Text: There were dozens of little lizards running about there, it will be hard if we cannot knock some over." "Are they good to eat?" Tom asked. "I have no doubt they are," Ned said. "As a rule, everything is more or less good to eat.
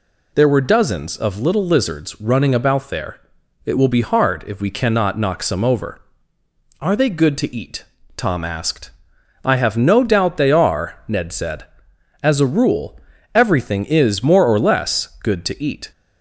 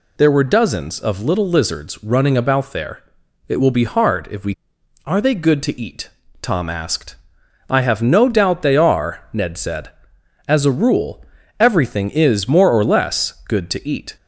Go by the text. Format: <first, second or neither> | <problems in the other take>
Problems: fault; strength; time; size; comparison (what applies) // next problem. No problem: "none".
first | skips "cannot knock some over"; at 4.7 s